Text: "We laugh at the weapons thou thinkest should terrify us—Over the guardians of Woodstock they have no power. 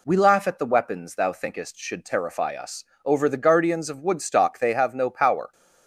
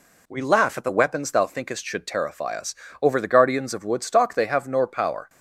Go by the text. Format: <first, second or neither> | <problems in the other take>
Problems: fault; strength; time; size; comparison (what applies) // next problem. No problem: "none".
first | says "nor" for "no"; at 4.6 s